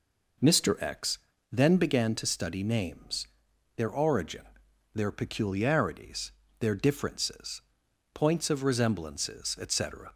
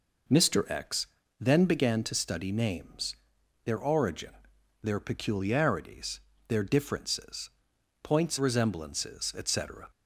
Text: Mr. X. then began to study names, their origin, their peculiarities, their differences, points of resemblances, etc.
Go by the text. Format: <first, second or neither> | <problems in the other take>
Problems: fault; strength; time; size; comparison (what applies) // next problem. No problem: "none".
first | pauses between "X" and "then"; slight; at 1.0 s; 0.32 s long; slight in the first // skips "of"; at 8.3 s